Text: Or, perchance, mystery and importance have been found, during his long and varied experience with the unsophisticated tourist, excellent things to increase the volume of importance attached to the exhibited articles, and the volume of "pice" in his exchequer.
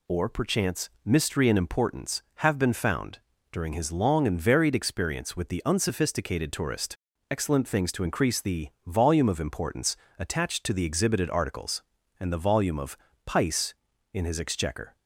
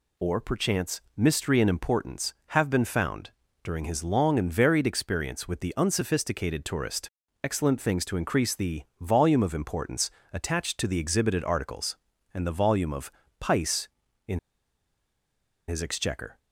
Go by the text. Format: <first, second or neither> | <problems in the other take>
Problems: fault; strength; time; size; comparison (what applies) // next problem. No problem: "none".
first | pauses between "the" and "volume"; slight; at 8.8 s; 0.16 s long; slight in the first // pauses between "importance" and "attached"; slight; at 10.0 s; 0.24 s long; slight in the first // pauses between "of" and "pice"; slight; at 13.1 s; 0.28 s long; slight in the first // pauses between "in" and "his"; strong; at 14.3 s; 1.2 s long